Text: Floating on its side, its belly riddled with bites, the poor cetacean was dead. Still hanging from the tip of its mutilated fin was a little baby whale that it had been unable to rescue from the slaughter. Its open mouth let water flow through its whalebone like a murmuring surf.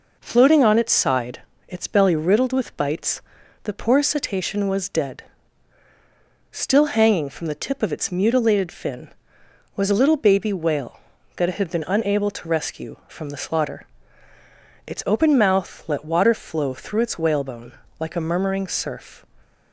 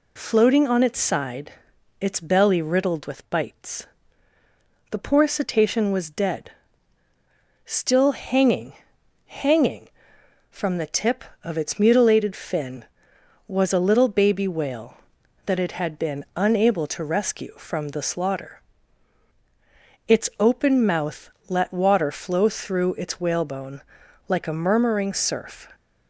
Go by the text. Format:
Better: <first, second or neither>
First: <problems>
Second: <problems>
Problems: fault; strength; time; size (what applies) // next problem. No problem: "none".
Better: first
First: pauses between "whalebone" and "like"; slight; at 17.7 s; 0.28 s long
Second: says "hanging" twice; at 9.2 s // pauses between "mouth" and "let"; slight; at 21.2 s; 0.18 s long // pauses between "whalebone" and "like"; noticeable; at 23.8 s; 0.46 s long